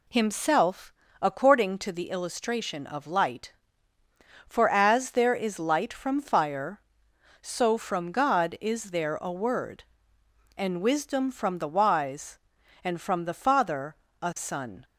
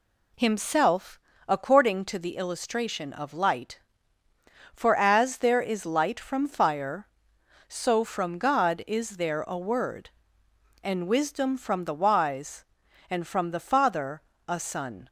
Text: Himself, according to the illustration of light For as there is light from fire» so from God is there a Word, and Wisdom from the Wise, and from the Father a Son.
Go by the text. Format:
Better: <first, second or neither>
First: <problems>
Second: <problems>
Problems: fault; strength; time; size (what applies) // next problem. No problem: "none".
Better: neither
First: pauses between "Father" and "a"; slight; at 13.9 s; 0.26 s long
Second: pauses between "Father" and "a"; slight; at 14.2 s; 0.26 s long